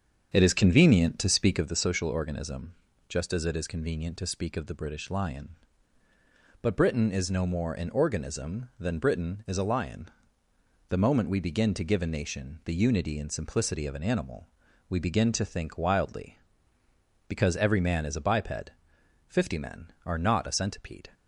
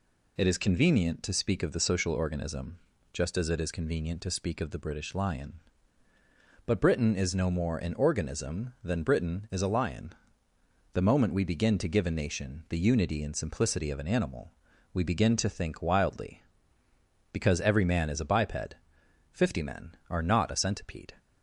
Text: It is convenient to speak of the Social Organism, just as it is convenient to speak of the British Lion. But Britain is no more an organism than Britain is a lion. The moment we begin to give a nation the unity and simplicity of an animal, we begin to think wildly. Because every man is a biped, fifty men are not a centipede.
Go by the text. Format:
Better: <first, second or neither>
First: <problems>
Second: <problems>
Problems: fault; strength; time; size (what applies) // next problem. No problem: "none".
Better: second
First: starts louder than the rest; strong; until 1.7 s; 7 dB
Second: none